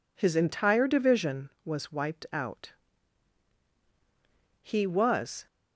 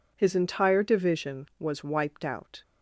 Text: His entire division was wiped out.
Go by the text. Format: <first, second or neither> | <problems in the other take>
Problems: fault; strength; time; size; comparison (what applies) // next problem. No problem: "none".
second | goes on to say "He was"; noticeable; from 4.6 s on; 0.84 s long